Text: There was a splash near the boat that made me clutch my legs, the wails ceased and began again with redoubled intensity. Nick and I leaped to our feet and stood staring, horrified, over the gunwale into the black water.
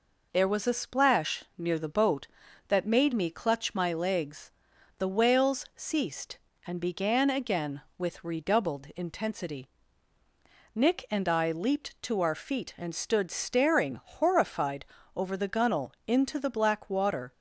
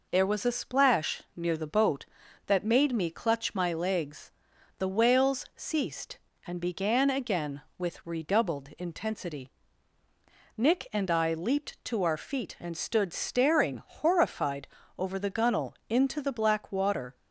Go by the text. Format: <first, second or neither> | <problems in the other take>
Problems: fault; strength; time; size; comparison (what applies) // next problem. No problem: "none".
neither | none